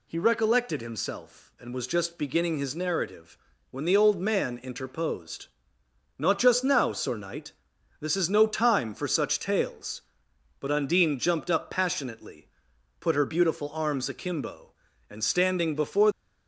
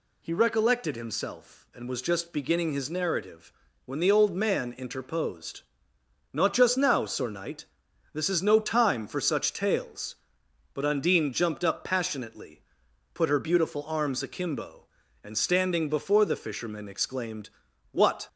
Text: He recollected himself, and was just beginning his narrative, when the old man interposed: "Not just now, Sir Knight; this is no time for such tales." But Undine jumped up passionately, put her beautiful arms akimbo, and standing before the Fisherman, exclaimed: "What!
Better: second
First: stops before "the Fisherman exclaimed What"; at 16.1 s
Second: none

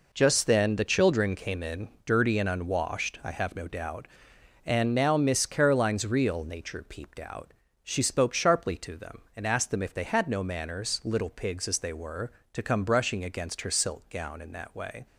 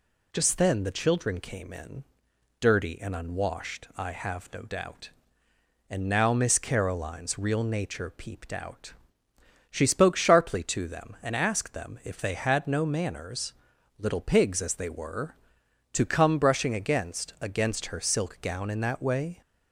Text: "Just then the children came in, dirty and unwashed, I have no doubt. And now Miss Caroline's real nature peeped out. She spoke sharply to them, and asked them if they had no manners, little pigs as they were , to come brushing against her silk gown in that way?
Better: first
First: none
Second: says "against" twice; at 17.4 s

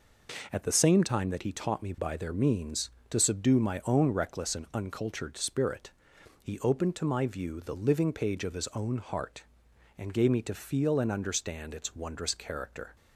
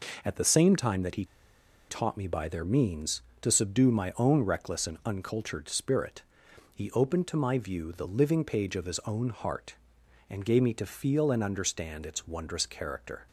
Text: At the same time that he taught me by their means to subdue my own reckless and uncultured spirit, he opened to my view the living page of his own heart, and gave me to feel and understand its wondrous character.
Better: first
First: none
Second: pauses between "he" and "taught"; noticeable; at 1.2 s; 0.64 s long

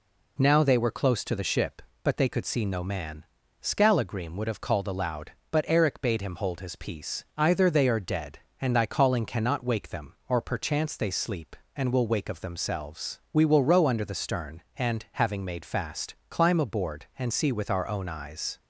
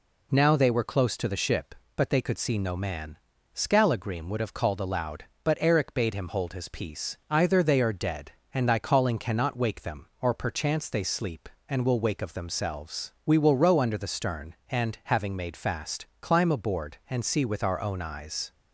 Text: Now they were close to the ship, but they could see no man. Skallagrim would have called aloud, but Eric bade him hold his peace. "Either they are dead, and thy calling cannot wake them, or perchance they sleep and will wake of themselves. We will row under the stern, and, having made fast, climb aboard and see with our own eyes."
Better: neither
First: none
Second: none

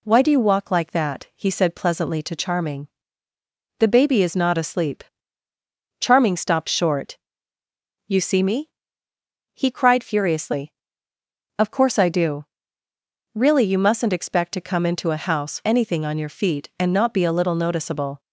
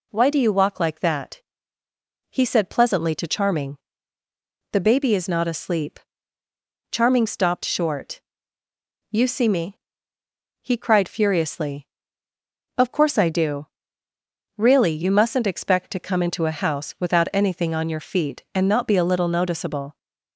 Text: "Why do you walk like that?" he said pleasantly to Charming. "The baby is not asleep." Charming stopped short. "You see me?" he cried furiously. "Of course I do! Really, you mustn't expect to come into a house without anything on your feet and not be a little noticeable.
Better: second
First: skips "without"; at 15.6 s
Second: none

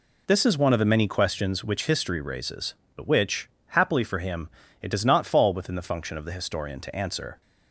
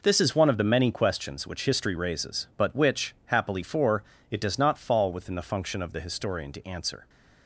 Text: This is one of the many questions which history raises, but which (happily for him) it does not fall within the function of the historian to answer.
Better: first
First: none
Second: skips "him"; at 4.1 s

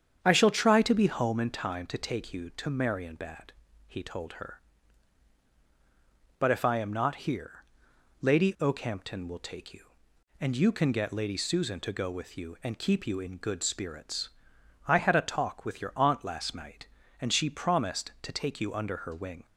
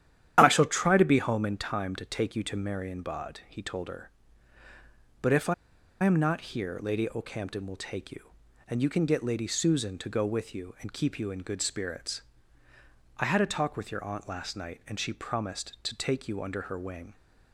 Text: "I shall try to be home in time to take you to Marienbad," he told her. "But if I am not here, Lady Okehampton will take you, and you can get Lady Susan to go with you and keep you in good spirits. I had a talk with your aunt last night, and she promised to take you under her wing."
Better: first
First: starts louder than the rest; strong; until 1.2 s; 8 dB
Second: starts louder than the rest; strong; until 1.3 s; 10.5 dB // pauses between "I" and "am"; noticeable; at 5.5 s; 0.49 s long

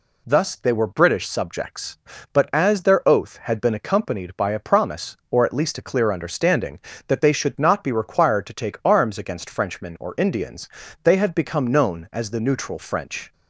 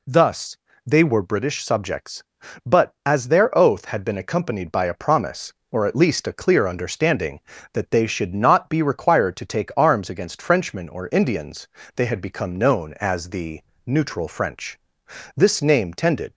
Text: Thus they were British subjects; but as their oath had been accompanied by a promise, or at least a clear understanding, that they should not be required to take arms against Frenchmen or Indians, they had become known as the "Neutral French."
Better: first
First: none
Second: pauses between "Thus" and "they"; slight; at 0.5 s; 0.26 s long // pauses between "the" and "Neutral"; slight; at 13.6 s; 0.24 s long // goes on to say "This name tended"; noticeable; from 15.3 s on; 0.98 s long

